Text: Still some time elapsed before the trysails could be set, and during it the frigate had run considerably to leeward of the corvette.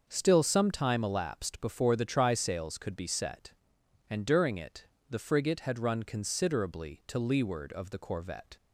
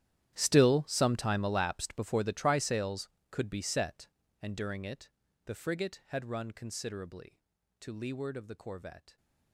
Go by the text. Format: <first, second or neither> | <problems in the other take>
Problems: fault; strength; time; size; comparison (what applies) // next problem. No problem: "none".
first | gets quieter; strong; throughout; 18.5 dB // starts louder than the rest; strong; until 1.3 s; 11.5 dB; also in the first // pauses between "it" and "the"; slight; at 5.1 s; 0.34 s long; slight in the first